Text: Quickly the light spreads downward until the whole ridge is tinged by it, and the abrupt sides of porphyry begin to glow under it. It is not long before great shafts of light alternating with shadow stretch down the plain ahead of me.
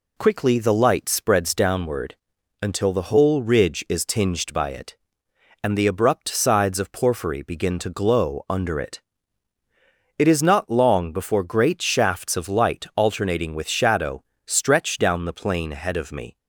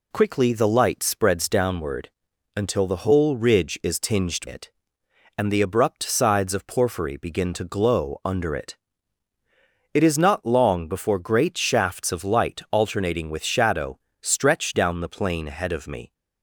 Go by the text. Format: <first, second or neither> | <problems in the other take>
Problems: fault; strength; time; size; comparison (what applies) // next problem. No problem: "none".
first | pauses between "downward" and "until"; noticeable; at 2.0 s; 0.48 s long; noticeable in the first // skips "by"; at 4.4 s // pauses between "shadow" and "stretch"; slight; at 13.9 s; 0.22 s long; slight in the first